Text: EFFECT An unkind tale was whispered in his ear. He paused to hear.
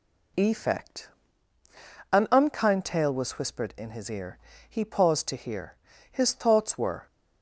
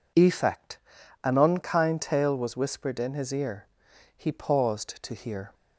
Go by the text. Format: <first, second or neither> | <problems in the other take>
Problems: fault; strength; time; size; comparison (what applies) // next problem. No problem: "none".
second | pauses between "EFFECT" and "An"; at 1.0 s; 1.0 s long; noticeable in the second // goes on to say "His thoughts were"; noticeable; from 6.0 s on; 0.96 s long